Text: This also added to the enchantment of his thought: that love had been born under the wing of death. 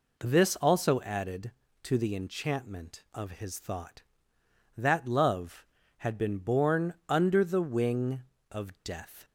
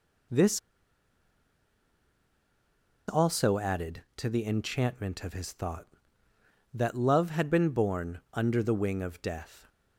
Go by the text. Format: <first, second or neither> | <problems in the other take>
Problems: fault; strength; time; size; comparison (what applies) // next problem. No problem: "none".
first | pauses between "This" and "also"; strong; at 0.5 s; 2.4 s long